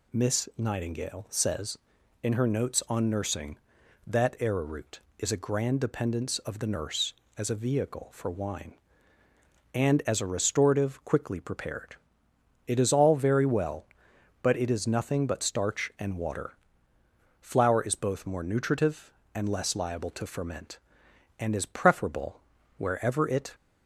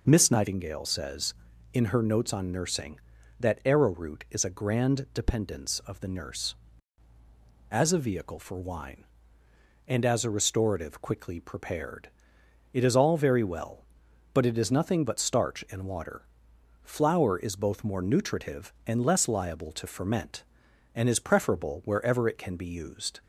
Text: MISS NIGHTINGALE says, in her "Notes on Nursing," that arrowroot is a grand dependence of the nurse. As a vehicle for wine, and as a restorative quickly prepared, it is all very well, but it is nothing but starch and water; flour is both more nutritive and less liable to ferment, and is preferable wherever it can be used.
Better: second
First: pauses between "preferable" and "wherever"; at 22.3 s; 0.38 s long // stops before "can be used"; at 23.5 s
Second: none

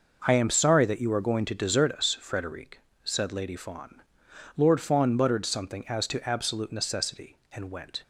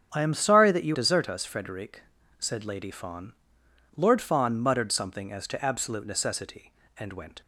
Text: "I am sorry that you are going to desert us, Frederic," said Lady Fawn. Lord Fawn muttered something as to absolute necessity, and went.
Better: first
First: none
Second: starts louder than the rest; strong; until 1.1 s; 8 dB // skips "are going to"; at 0.9 s

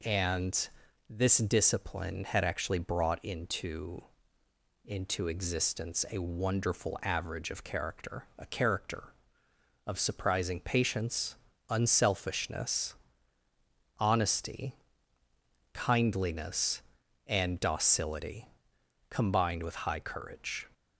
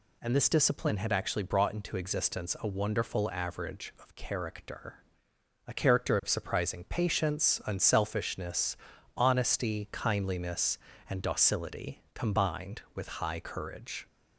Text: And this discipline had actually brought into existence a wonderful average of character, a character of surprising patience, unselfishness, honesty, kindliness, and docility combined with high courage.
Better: second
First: pauses between "And" and "this"; at 0.6 s; 0.40 s long // says "into" twice; at 4.8 s // pauses between "docility" and "combined"; noticeable; at 18.4 s; 0.64 s long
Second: none

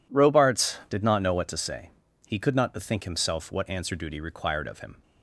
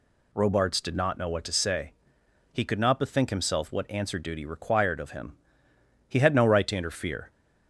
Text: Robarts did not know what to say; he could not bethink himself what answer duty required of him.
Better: first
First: none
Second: goes on to say "He had no right to interfere"; noticeable; from 6.0 s on; 1.2 s long

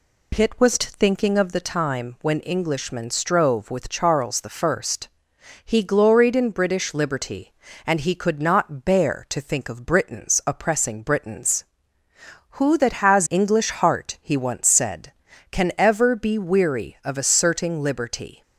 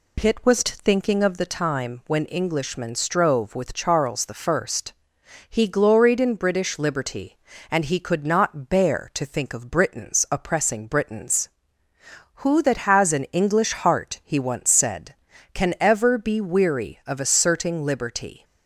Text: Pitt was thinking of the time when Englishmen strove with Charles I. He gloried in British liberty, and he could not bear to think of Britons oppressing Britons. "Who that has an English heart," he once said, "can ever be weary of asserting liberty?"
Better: second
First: skips "an"; at 13.2 s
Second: none

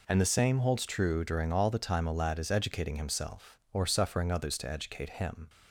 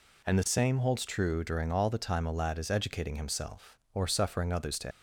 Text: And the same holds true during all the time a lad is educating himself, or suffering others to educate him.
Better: first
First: none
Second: stops before "educate him"; at 4.9 s

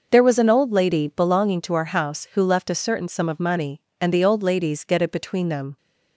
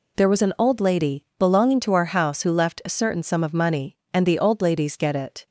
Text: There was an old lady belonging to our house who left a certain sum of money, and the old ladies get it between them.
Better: first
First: none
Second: stops before "between them"; at 5.4 s

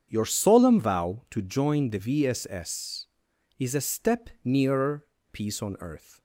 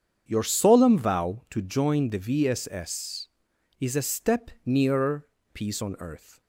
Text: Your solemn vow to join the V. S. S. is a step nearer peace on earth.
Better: neither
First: starts louder than the rest; strong; until 1.1 s; 7.5 dB // pauses between "nearer" and "peace"; slight; at 5.0 s; 0.28 s long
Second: starts louder than the rest; strong; until 1.2 s; 7.5 dB // pauses between "nearer" and "peace"; slight; at 5.2 s; 0.28 s long

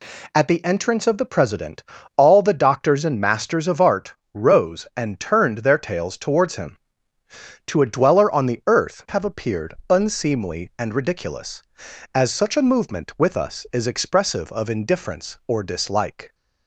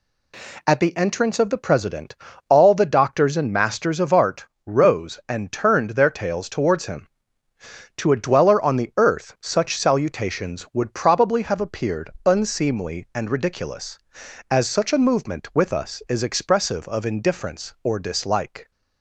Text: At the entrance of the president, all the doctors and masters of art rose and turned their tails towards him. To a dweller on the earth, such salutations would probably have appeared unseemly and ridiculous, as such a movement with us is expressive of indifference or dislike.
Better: second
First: pauses between "art" and "rose"; slight; at 4.1 s; 0.20 s long // skips "such salutations would probably"; at 9.0 s // pauses between "appeared" and "unseemly"; slight; at 9.7 s; 0.16 s long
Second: pauses between "art" and "rose"; slight; at 4.4 s; 0.20 s long // pauses between "appeared" and "unseemly"; slight; at 12.0 s; 0.16 s long

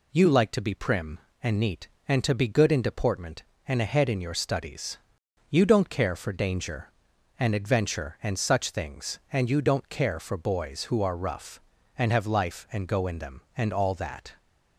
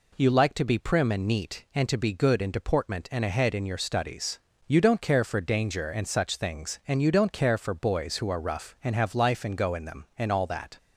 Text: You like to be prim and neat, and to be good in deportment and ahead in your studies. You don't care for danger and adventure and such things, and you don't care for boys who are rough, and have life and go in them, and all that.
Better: first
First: none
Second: skips "and adventure"; at 5.8 s

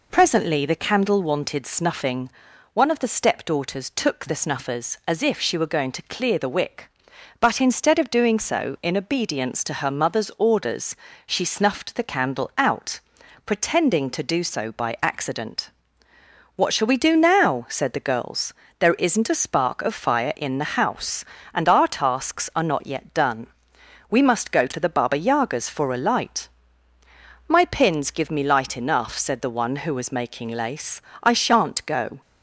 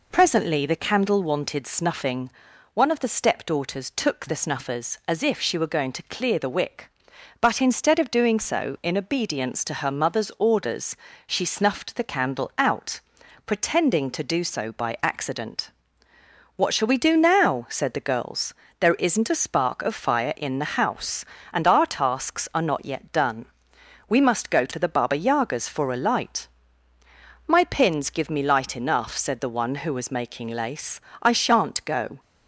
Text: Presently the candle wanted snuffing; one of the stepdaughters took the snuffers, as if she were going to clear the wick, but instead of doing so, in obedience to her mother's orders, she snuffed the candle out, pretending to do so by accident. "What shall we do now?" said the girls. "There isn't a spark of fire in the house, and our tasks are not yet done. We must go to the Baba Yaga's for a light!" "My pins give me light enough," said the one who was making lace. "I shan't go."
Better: neither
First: none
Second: none

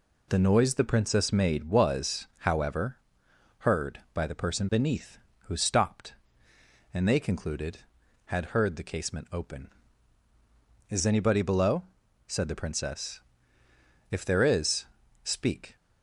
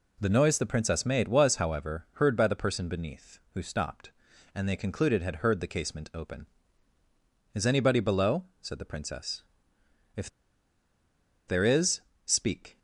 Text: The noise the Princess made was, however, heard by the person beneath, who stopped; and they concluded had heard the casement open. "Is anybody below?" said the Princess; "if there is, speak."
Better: first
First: none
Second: pauses between "if" and "there"; at 10.2 s; 1.1 s long

